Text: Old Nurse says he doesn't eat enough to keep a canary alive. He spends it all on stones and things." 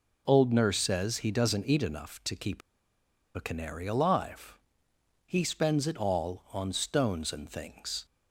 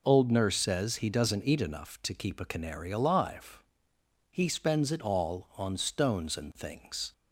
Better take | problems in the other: second | pauses between "keep" and "a"; noticeable; at 2.6 s; 0.76 s long

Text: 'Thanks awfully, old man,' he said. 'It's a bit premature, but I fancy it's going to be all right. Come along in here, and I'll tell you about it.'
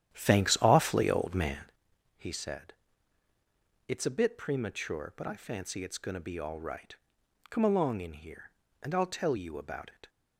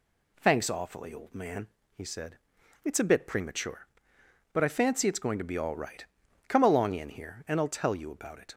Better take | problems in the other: second | starts louder than the rest; strong; until 1.8 s; 10.5 dB

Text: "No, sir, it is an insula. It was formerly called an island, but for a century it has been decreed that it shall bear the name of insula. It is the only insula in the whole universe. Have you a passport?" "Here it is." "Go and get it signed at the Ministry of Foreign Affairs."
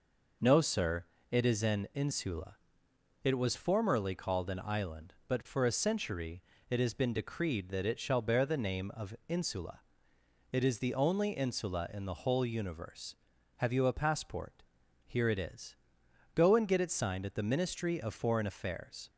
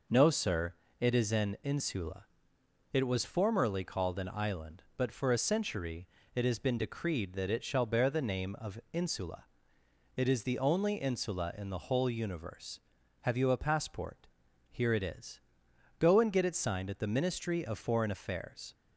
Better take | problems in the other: neither | pauses between "century" and "it"; slight; the same in both

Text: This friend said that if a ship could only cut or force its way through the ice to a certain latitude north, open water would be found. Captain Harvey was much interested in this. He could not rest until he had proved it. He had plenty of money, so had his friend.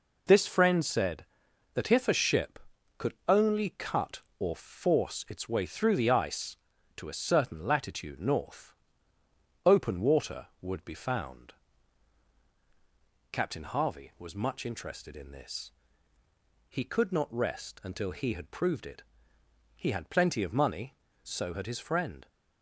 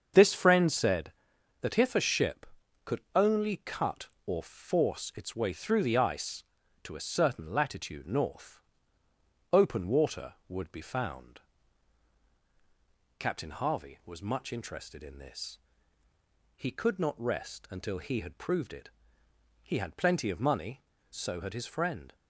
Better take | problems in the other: first | starts louder than the rest; until 1.3 s; 7 dB // pauses between "could" and "only"; slight; at 3.0 s; 0.16 s long; slight in the first

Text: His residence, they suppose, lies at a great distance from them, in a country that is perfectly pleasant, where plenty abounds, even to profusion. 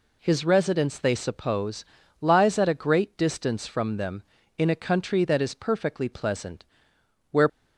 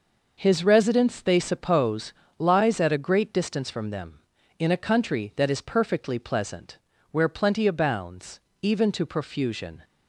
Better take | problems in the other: second | stops before "plenty abounds even to profusion"; at 7.4 s

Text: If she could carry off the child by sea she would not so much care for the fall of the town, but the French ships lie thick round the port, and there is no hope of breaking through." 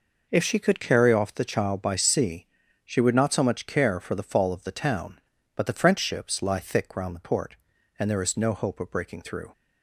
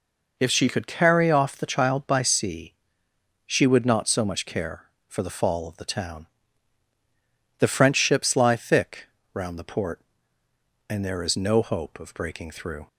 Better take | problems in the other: first | pauses between "sea" and "she"; noticeable; at 2.7 s; 0.74 s long; also in the first // skips "but"; at 6.9 s // pauses between "thick" and "round"; slight; at 9.0 s; 0.30 s long

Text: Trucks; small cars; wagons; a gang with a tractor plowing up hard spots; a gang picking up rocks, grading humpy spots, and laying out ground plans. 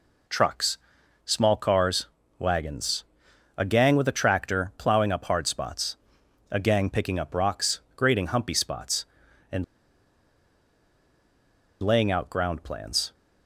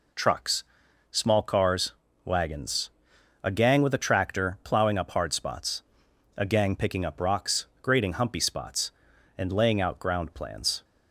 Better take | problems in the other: second | pauses between "and" and "laying"; strong; at 9.6 s; 2.1 s long

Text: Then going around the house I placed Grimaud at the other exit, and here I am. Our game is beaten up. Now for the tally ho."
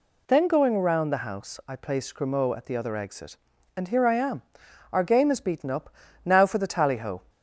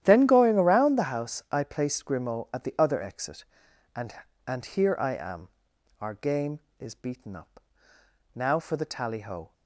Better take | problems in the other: first | starts louder than the rest; strong; until 1.0 s; 11.5 dB // says "and" twice; at 4.4 s

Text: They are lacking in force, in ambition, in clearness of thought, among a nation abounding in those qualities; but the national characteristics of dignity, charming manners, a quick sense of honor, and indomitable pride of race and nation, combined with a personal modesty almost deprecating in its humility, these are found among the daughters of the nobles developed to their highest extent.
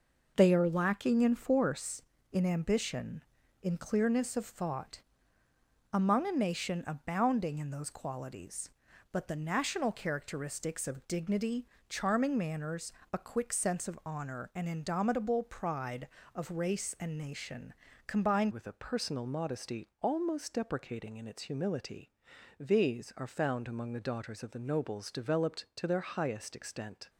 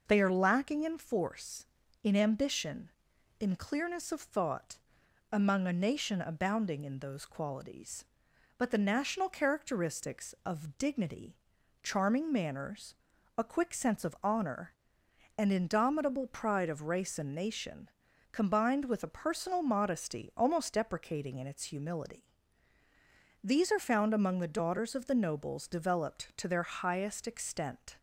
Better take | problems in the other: second | changes voice at "with"; from 18.5 s on; 8.5 s long // pauses between "modesty" and "almost"; slight; at 19.8 s; 0.16 s long

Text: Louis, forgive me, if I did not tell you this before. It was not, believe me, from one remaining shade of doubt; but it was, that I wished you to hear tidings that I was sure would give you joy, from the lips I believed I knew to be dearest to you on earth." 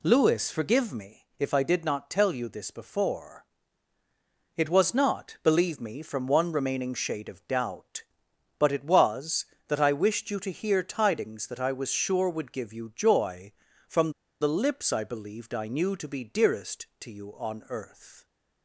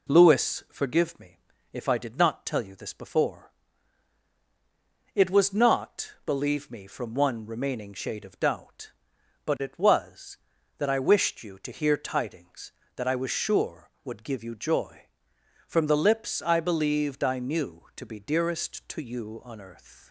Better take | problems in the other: second | pauses between "from" and "the"; slight; at 14.1 s; 0.28 s long

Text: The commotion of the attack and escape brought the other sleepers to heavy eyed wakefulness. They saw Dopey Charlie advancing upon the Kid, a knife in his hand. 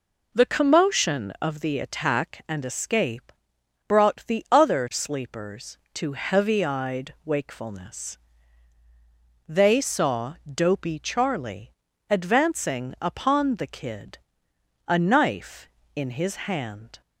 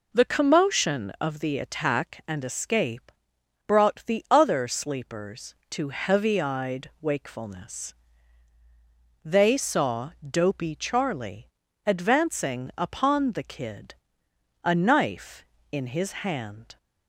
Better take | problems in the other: neither | pauses between "escape" and "brought"; noticeable; the same in both // pauses between "saw" and "Dopey"; slight; the same in both // pauses between "Charlie" and "advancing"; slight; the same in both

